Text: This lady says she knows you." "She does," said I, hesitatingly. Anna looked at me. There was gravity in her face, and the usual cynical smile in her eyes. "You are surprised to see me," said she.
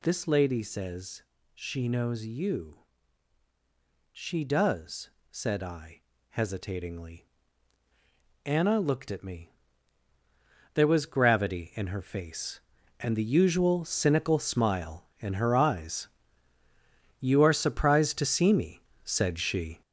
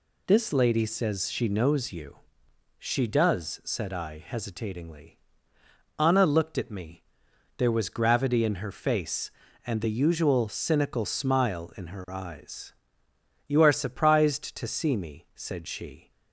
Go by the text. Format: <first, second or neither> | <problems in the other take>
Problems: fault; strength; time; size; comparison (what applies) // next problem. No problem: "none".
second | gets louder; throughout; 6.5 dB // pauses between "says" and "she"; slight; at 1.2 s; 0.32 s long